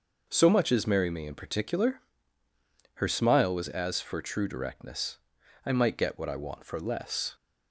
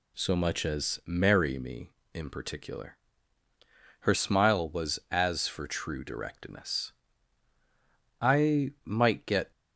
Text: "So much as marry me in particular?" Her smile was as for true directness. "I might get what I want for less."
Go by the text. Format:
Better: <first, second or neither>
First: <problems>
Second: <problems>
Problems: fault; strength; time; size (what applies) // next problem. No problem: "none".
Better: first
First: none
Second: stops before "what I want for less"; at 9.5 s